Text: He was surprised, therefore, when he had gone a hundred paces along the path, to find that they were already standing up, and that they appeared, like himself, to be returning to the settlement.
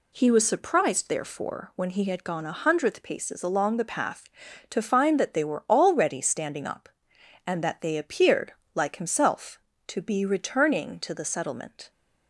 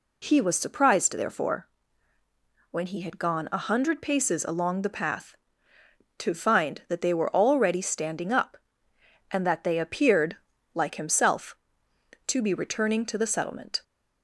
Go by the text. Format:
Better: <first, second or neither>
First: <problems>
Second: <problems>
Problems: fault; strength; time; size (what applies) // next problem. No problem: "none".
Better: second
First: says "hundredth" for "hundred"; at 2.5 s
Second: none